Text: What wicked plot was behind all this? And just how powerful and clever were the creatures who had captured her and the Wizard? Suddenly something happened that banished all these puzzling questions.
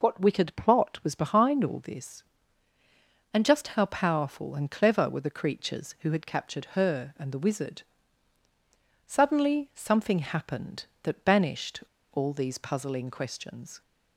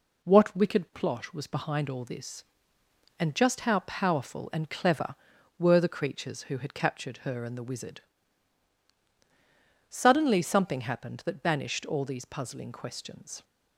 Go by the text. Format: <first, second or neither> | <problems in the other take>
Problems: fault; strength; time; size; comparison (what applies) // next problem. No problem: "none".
second | pauses between "banished" and "all"; slight; at 11.8 s; 0.29 s long